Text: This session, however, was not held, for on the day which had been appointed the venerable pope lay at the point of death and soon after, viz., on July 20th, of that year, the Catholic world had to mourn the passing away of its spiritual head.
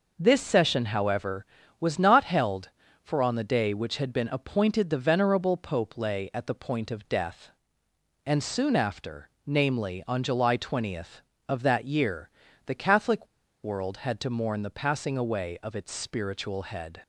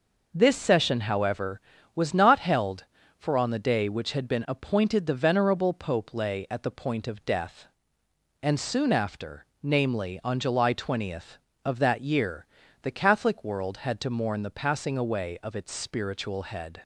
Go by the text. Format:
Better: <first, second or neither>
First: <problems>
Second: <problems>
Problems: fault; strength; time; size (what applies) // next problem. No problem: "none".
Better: second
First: pauses between "Catholic" and "world"; at 13.2 s; 0.37 s long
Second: none